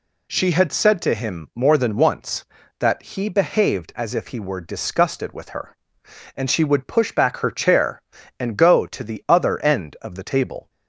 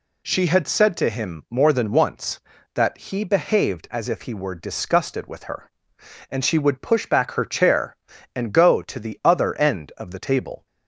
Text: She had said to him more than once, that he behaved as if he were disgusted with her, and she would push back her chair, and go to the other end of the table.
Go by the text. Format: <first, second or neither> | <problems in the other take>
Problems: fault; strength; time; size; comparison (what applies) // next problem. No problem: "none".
neither | none